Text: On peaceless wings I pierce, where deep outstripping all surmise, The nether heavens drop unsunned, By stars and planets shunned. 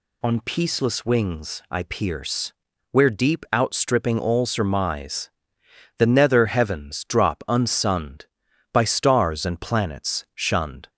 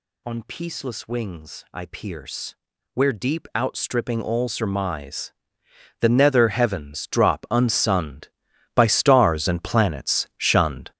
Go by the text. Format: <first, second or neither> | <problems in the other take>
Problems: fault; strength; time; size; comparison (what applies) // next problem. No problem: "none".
first | gets louder; strong; throughout; 9.5 dB